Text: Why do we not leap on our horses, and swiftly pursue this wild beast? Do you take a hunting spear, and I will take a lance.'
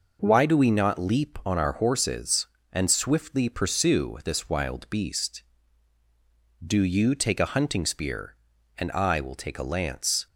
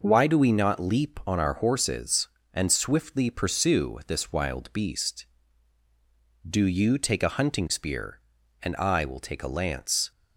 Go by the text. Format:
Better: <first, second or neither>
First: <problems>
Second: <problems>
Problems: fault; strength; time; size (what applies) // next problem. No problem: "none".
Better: neither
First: none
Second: none